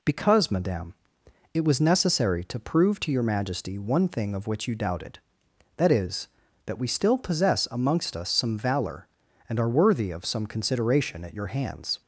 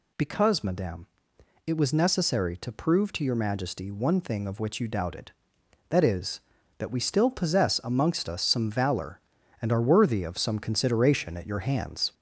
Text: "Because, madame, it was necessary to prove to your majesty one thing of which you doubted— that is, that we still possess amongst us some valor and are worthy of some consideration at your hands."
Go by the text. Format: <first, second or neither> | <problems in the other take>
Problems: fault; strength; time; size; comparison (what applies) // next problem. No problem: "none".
first | gets louder; throughout; 3.5 dB